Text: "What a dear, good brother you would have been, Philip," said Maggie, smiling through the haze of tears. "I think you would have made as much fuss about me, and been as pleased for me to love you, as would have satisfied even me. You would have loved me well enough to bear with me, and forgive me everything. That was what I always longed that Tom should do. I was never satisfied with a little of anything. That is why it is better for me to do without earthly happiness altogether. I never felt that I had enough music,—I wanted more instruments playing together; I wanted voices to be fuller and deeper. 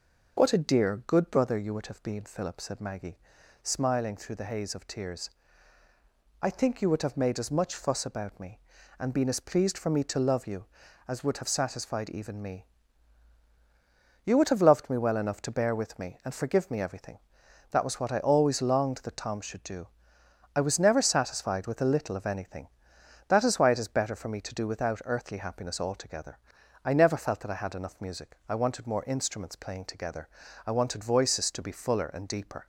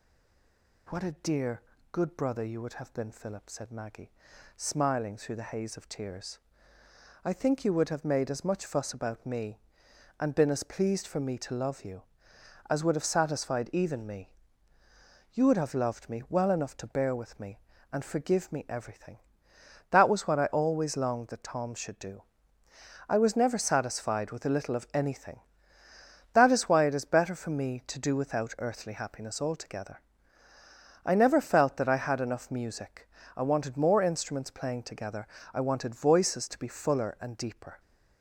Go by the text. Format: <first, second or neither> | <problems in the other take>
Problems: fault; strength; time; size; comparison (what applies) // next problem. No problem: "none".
first | stays silent before the first word; slight; until 0.8 s; 0.8 s long